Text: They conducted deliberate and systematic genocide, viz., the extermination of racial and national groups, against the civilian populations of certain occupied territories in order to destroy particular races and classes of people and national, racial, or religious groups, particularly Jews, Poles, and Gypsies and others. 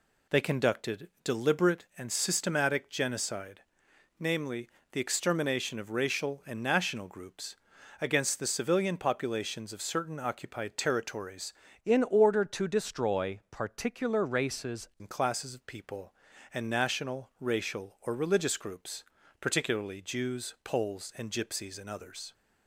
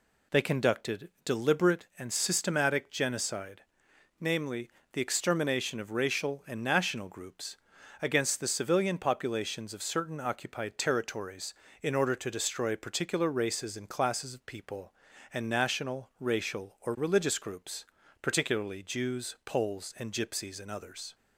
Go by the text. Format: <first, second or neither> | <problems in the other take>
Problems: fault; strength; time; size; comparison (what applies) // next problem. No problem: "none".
second | changes voice from "in" to "races"; from 11.8 to 14.8 s; 3.0 s long